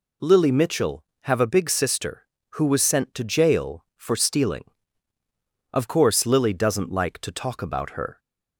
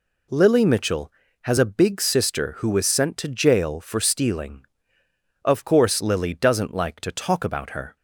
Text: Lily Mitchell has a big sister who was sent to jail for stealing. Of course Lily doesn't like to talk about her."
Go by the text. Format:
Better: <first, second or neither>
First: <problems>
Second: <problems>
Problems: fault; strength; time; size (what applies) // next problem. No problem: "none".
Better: second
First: says "have" for "has"; at 1.2 s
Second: none